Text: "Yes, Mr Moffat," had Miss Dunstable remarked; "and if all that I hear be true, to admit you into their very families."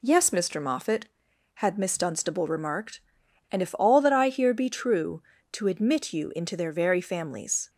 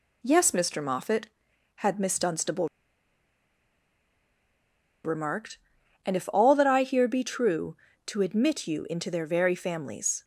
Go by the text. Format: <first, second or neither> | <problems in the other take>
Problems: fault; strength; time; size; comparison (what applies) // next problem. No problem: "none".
first | pauses between "Dunstable" and "remarked"; strong; at 2.6 s; 2.3 s long